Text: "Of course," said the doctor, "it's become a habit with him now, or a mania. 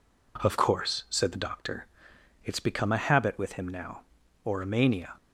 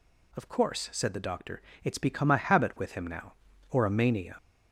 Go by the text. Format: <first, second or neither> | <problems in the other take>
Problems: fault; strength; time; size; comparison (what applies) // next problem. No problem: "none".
first | gets louder; throughout; 3.5 dB